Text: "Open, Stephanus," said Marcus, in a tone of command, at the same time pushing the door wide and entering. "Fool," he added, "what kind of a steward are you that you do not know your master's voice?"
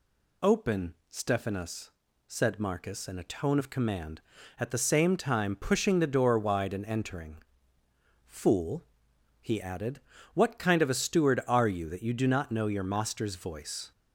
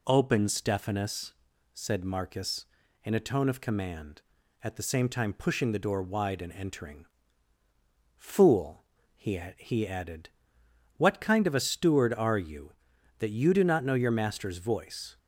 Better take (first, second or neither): first